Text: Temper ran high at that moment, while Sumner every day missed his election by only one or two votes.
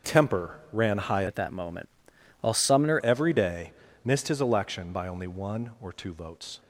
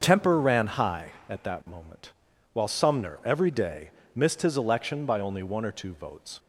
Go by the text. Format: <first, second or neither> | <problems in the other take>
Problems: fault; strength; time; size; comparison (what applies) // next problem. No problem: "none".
second | starts louder than the rest; until 1.1 s; 6.5 dB; also in the second // changes voice from "at" to "Sumner"; from 1.2 to 2.9 s; 1.7 s long // pauses between "day" and "missed"; slight; at 3.7 s; 0.32 s long; slight in the second